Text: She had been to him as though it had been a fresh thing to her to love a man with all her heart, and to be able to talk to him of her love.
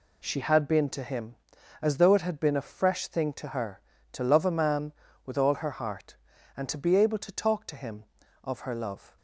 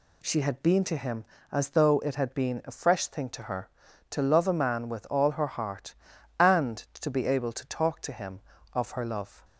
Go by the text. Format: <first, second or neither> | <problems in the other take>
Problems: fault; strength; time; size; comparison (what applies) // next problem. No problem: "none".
neither | none